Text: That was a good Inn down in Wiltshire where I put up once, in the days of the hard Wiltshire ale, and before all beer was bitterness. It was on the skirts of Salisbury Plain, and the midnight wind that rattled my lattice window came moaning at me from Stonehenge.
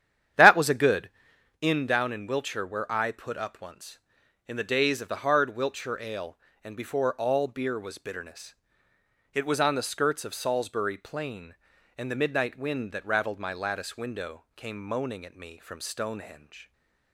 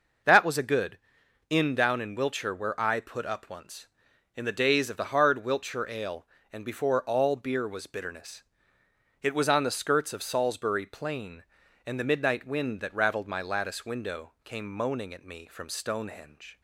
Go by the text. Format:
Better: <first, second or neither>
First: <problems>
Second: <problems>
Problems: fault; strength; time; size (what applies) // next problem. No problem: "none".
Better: second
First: starts louder than the rest; strong; until 1.6 s; 10 dB // pauses between "good" and "Inn"; noticeable; at 1.0 s; 0.50 s long // stays silent after the last word; slight; from 16.6 s on; 0.5 s long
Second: pauses between "good" and "Inn"; noticeable; at 0.9 s; 0.50 s long